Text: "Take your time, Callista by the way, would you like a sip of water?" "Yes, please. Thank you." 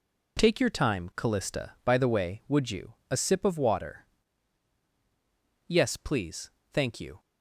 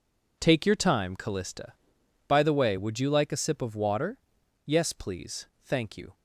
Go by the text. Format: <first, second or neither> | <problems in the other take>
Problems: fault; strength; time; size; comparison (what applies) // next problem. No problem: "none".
second | skips "like"; at 3.0 s